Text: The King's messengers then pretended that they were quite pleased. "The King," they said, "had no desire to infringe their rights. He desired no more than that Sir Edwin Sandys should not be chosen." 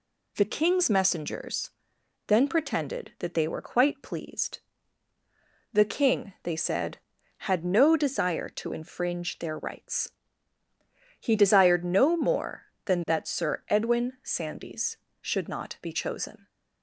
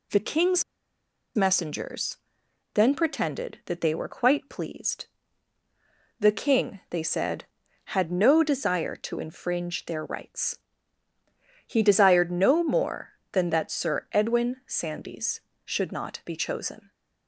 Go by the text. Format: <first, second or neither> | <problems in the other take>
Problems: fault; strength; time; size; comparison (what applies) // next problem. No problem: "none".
first | pauses between "King's" and "messengers"; noticeable; at 0.6 s; 0.72 s long // pauses between "messengers" and "then"; noticeable; at 2.1 s; 0.56 s long; noticeable in the first